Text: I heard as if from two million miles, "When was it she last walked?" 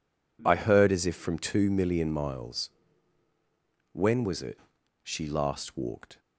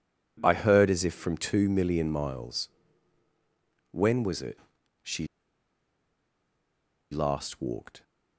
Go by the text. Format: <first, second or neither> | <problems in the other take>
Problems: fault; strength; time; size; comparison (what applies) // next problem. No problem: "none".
first | pauses between "it" and "she"; noticeable; at 4.5 s; 0.46 s long; noticeable in the first // pauses between "she" and "last"; strong; at 5.2 s; 1.8 s long